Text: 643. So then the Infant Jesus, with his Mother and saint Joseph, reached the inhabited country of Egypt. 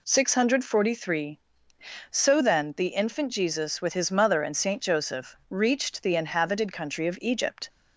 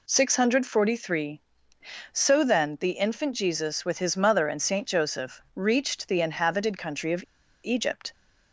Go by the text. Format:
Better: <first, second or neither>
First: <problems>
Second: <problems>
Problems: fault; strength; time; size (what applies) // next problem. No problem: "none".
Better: first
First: none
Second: pauses between "of" and "Egypt"; at 7.2 s; 0.39 s long